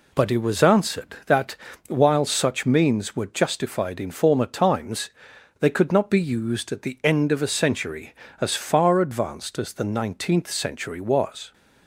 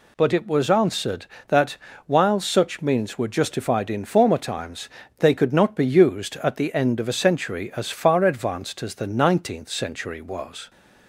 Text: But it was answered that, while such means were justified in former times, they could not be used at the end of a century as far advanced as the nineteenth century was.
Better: neither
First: none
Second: none

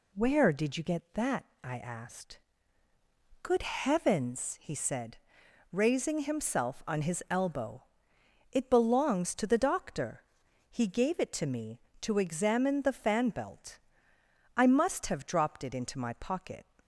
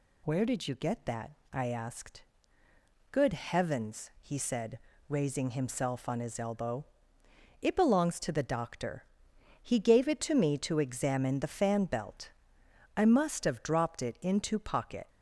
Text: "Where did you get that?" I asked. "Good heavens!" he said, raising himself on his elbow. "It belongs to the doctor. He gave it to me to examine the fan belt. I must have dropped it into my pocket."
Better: first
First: none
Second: skips "my"; at 14.5 s

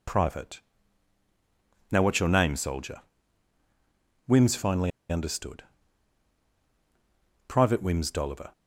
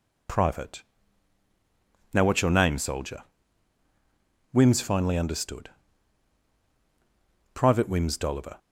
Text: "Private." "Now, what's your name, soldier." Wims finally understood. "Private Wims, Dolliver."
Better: second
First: pauses between "finally" and "understood"; slight; at 4.9 s; 0.19 s long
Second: none

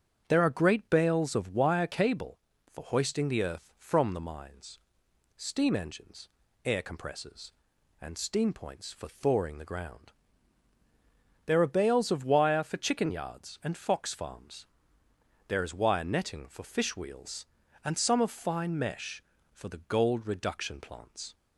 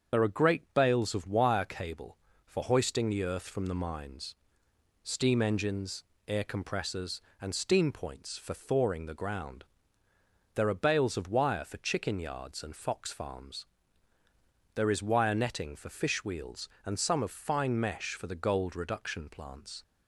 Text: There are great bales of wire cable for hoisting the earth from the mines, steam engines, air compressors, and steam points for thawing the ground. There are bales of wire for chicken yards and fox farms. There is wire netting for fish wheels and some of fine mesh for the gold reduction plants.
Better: first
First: starts louder than the rest; strong; until 1.2 s; 8 dB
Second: loses the start of "There"; at 0.1 s; 40 ms // starts louder than the rest; strong; until 1.2 s; 7 dB

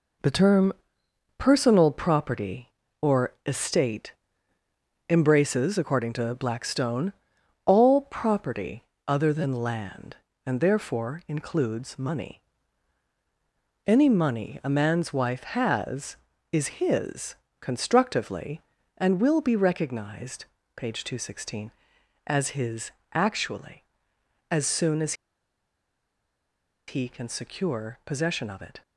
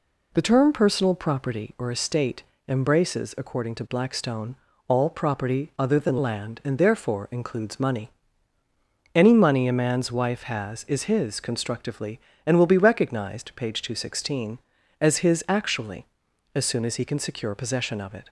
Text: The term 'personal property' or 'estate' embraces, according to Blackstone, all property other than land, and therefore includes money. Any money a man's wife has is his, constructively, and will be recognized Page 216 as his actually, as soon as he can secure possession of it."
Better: second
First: pauses between "term" and "personal"; noticeable; at 0.7 s; 0.64 s long // pauses between "estate" and "embraces"; noticeable; at 4.1 s; 0.96 s long // pauses between "property" and "other"; slight; at 8.8 s; 0.24 s long // pauses between "recognized" and "Page"; slight; at 20.4 s; 0.32 s long // pauses between "his" and "actually"; slight; at 22.9 s; 0.22 s long // pauses between "as" and "he"; strong; at 25.1 s; 1.7 s long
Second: pauses between "estate" and "embraces"; slight; at 2.4 s; 0.24 s long

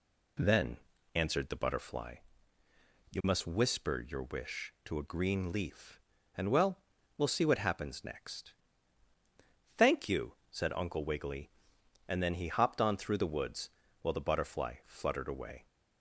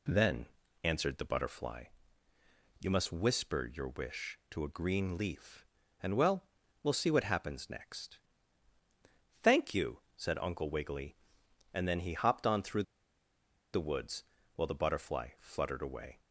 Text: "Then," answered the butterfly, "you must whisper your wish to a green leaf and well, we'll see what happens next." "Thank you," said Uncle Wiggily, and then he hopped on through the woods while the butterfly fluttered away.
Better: first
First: pauses between "woods" and "while"; slight; at 13.6 s; 0.32 s long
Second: pauses between "through" and "the"; noticeable; at 12.8 s; 0.90 s long // pauses between "woods" and "while"; slight; at 14.2 s; 0.32 s long

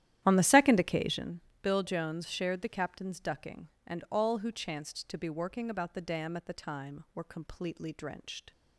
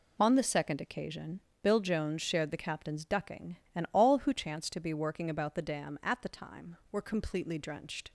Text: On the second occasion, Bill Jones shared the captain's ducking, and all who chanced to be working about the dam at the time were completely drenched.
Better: second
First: starts louder than the rest; strong; until 1.3 s; 12 dB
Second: none

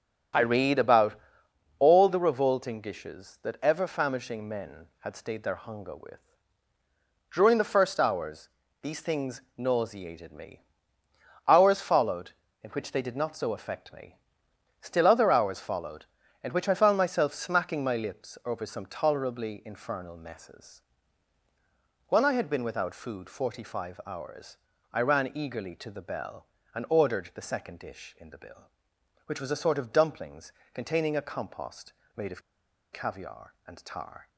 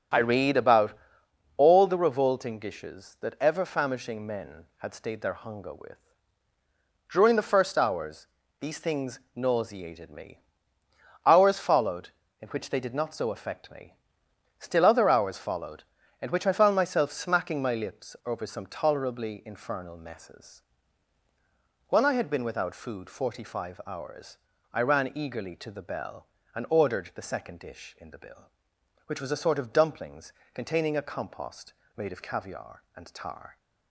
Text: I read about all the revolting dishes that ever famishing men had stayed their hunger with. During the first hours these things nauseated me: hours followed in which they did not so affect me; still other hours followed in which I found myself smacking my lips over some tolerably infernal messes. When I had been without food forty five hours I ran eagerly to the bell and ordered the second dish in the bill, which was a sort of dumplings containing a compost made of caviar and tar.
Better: second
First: starts louder than the rest; until 1.9 s; 6.5 dB // pauses between "about" and "all"; noticeable; at 1.1 s; 0.64 s long // pauses between "hours" and "these"; slight; at 8.4 s; 0.34 s long // pauses between "hours" and "I"; slight; at 24.5 s; 0.36 s long // pauses between "dumplings" and "containing"; slight; at 30.5 s; 0.22 s long // pauses between "compost" and "made"; slight; at 31.9 s; 0.22 s long // pauses between "of" and "caviar"; noticeable; at 32.4 s; 0.52 s long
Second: starts louder than the rest; until 1.7 s; 6.5 dB // pauses between "about" and "all"; noticeable; at 0.9 s; 0.64 s long // pauses between "hours" and "these"; slight; at 8.2 s; 0.34 s long // pauses between "hours" and "I"; slight; at 24.3 s; 0.36 s long // pauses between "dumplings" and "containing"; slight; at 30.3 s; 0.22 s long // pauses between "compost" and "made"; slight; at 31.7 s; 0.22 s long

